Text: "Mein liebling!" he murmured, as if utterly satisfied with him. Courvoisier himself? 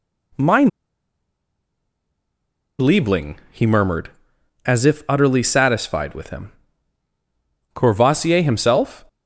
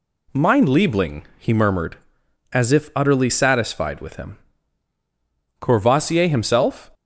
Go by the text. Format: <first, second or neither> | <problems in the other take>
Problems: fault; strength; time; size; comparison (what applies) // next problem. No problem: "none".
second | pauses between "Mein" and "liebling"; strong; at 0.6 s; 2.1 s long